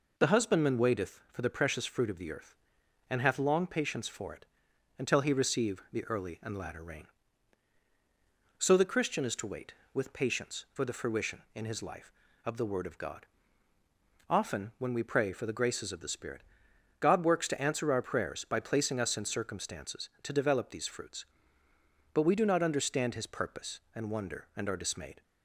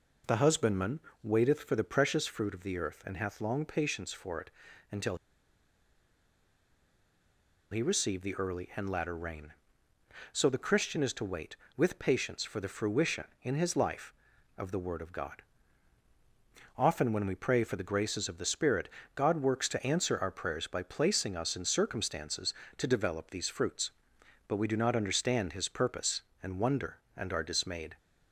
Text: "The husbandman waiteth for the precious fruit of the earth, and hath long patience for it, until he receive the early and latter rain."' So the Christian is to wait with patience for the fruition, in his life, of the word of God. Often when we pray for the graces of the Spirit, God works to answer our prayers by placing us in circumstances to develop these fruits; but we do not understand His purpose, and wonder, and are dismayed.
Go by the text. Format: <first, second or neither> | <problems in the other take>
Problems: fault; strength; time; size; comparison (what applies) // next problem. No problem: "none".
first | pauses between "husbandman" and "waiteth"; slight; at 1.0 s; 0.20 s long // pauses between "until" and "he"; strong; at 5.1 s; 2.5 s long